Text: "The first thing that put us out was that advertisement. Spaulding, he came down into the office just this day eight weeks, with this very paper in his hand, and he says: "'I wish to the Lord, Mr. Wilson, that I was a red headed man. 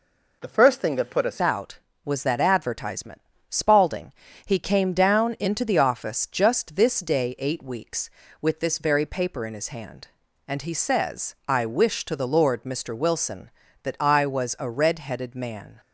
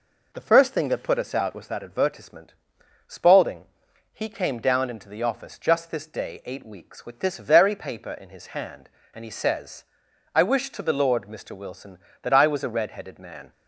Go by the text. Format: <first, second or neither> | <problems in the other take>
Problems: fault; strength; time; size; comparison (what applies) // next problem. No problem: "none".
second | changes voice at "out"; from 1.3 s on; 14.4 s long